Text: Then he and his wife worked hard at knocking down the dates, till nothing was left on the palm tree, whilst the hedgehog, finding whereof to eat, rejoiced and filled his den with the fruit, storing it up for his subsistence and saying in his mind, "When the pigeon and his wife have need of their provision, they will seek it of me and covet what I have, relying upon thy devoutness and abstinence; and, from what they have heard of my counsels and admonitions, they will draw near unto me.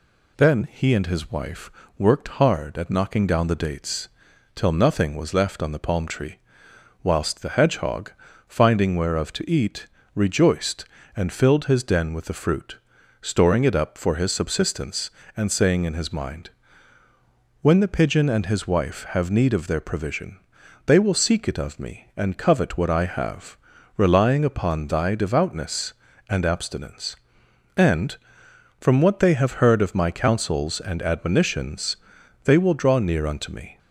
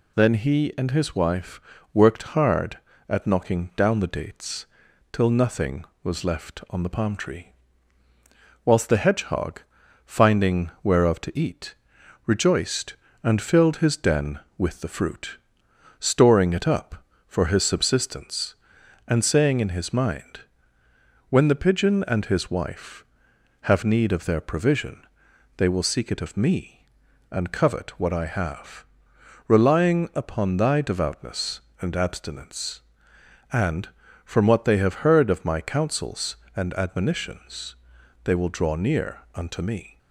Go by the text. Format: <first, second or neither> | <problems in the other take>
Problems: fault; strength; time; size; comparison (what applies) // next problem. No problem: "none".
neither | pauses between "wife" and "worked"; slight; the same in both